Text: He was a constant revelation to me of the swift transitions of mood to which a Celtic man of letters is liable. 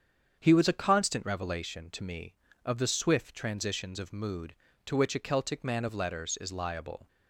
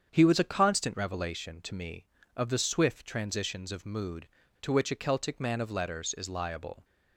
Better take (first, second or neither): neither